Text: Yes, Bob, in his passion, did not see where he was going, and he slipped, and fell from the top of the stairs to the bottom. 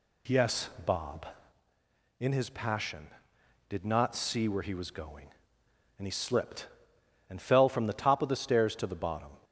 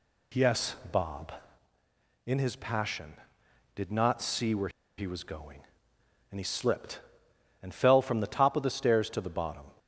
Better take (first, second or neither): first